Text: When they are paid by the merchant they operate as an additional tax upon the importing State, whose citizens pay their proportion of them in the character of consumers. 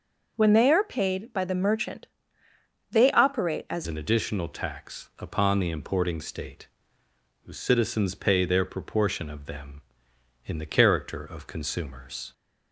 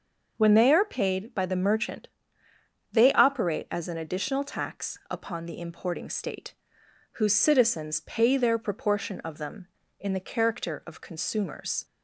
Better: second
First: pauses between "merchant" and "they"; noticeable; at 2.0 s; 0.84 s long // changes voice at "an"; from 3.8 s on; 8.5 s long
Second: pauses between "merchant" and "they"; noticeable; at 2.0 s; 0.84 s long

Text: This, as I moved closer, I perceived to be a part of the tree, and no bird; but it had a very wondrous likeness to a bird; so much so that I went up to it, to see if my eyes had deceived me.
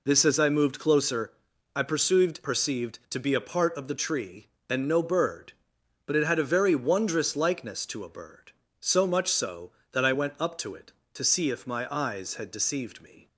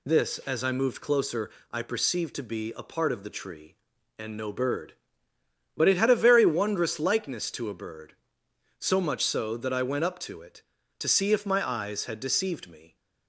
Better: second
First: says "perceived" twice; at 2.4 s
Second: none

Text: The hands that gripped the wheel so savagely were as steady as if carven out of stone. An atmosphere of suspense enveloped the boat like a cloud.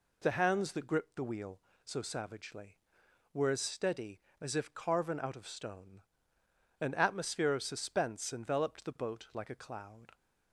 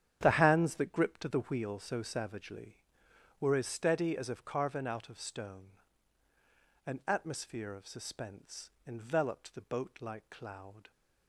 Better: first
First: none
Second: starts louder than the rest; strong; until 1.2 s; 9.5 dB // pauses between "suspense" and "enveloped"; slight; at 8.6 s; 0.17 s long // skips "a"; at 10.2 s

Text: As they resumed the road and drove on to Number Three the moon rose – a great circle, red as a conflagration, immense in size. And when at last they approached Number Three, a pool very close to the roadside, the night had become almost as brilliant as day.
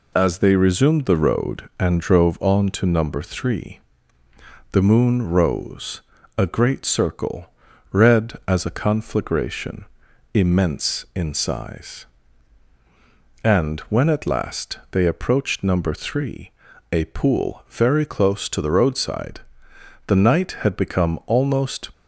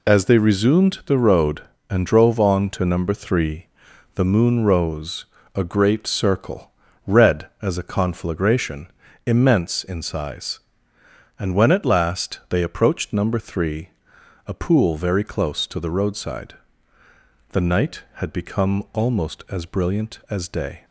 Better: second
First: pauses between "Three" and "the"; noticeable; at 3.7 s; 0.92 s long // stops before "as brilliant as day"; at 21.9 s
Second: pauses between "Three" and "the"; noticeable; at 3.6 s; 0.50 s long

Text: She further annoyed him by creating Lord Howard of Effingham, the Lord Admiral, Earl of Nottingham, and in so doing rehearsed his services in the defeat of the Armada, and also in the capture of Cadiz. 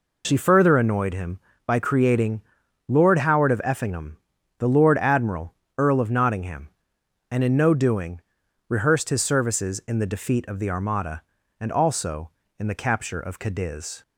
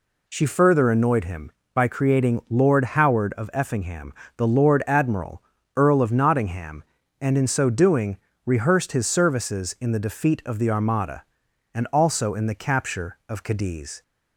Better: second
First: pauses between "creating" and "Lord"; noticeable; at 2.4 s; 0.46 s long // says "no" for "so"; at 7.5 s // pauses between "doing" and "rehearsed"; noticeable; at 8.1 s; 0.48 s long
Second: pauses between "doing" and "rehearsed"; slight; at 8.1 s; 0.28 s long

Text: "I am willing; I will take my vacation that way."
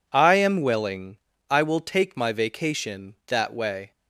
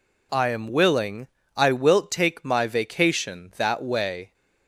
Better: first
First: none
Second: says "wilt" for "will"; at 1.7 s

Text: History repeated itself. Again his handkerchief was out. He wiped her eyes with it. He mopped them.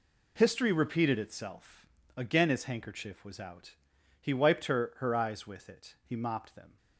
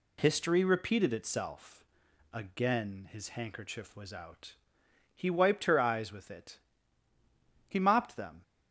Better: second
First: says "her" twice; at 4.9 s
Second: none

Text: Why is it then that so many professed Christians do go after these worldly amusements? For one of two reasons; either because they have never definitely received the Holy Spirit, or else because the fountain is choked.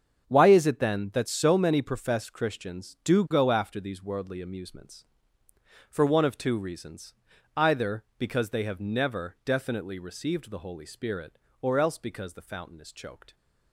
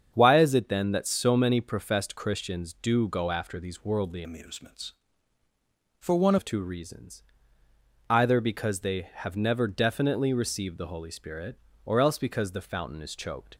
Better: first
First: starts louder than the rest; strong; until 1.2 s; 7.5 dB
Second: starts louder than the rest; strong; until 1.1 s; 7.5 dB // changes voice from "amusements" to "one"; from 4.2 to 6.3 s; 2.1 s long

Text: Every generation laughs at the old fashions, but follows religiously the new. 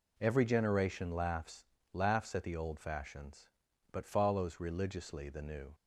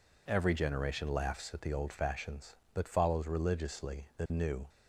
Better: second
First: says "laughs" twice; at 1.9 s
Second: none

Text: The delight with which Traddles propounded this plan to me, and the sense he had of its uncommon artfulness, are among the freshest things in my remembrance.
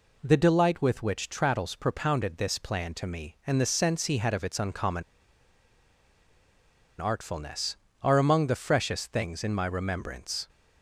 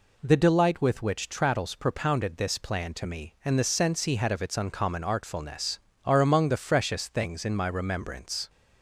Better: second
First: pauses between "uncommon" and "artfulness"; strong; at 5.0 s; 1.9 s long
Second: none

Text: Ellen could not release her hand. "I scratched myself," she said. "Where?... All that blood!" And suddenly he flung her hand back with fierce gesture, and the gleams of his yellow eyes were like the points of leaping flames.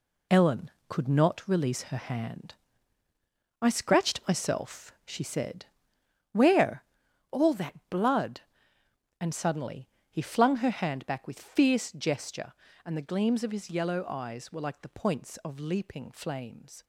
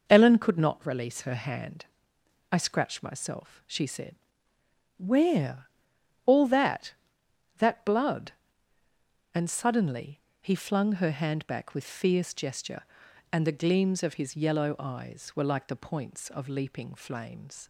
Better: first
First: pauses between "suddenly" and "he"; slight; at 9.8 s; 0.20 s long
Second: says "that" twice; at 7.5 s // pauses between "suddenly" and "he"; slight; at 10.1 s; 0.22 s long

